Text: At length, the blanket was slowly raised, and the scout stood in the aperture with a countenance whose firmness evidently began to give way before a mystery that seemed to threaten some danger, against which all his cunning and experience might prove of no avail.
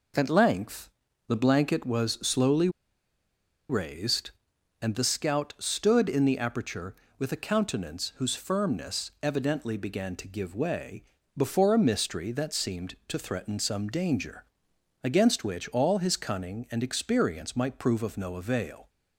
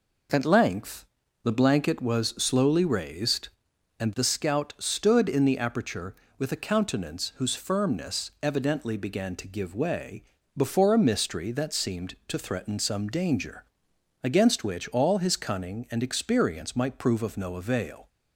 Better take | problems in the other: second | pauses between "slowly" and "raised"; at 2.6 s; 1.0 s long // pauses between "way" and "before"; slight; at 11.0 s; 0.34 s long; slight in the second

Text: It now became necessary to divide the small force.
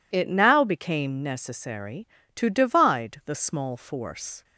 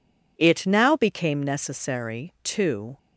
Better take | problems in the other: first | stops before "divide the small force"; at 2.9 s

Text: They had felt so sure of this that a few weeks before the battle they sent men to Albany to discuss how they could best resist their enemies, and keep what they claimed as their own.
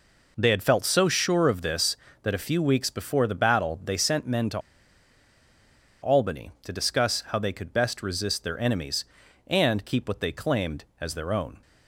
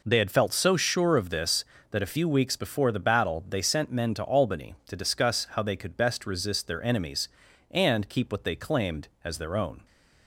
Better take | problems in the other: second | pauses between "to" and "Albany"; strong; at 4.5 s; 1.4 s long

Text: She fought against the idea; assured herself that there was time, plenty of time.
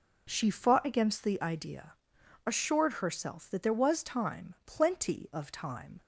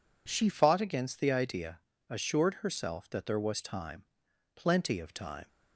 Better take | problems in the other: first | changes voice at "fought"; from 0.5 s on; 4.9 s long

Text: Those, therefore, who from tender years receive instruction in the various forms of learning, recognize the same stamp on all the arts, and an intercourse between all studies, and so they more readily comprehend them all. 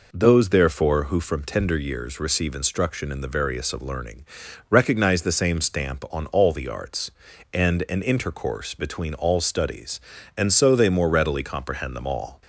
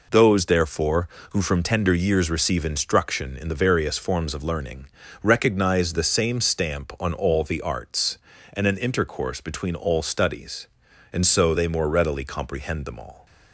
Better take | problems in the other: second | skips "forms"; at 3.7 s

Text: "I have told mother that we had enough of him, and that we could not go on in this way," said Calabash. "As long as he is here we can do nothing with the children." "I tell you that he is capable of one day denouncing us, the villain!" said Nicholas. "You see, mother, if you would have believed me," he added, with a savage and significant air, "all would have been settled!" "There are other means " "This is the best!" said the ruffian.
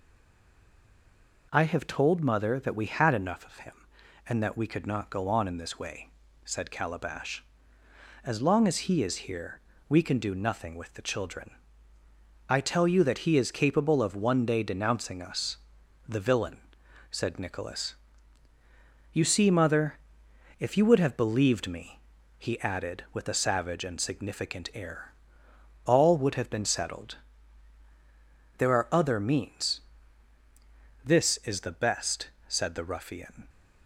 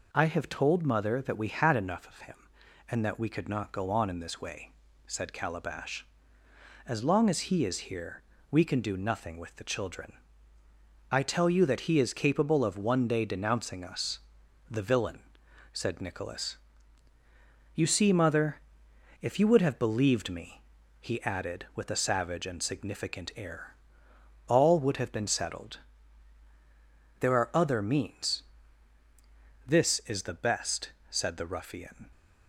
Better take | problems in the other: second | stays silent before the first word; noticeable; until 1.5 s; 1.5 s long // pauses between "here" and "we"; slight; at 9.5 s; 0.30 s long; slight in the second

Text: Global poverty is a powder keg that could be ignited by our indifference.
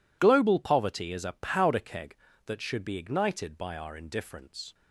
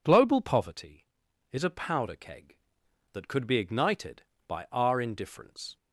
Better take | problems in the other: second | says "should" for "could"; at 2.6 s

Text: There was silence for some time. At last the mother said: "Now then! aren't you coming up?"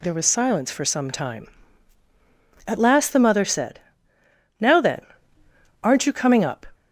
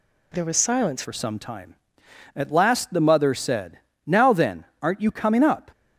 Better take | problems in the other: first | changes voice at "for"; from 1.0 s on; 4.7 s long

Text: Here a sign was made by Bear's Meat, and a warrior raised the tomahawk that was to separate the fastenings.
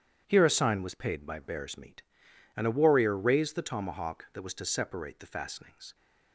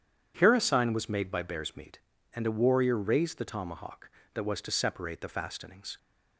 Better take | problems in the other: second | starts louder than the rest; strong; until 1.2 s; 9.5 dB // says "paid" for "made"; at 0.9 s

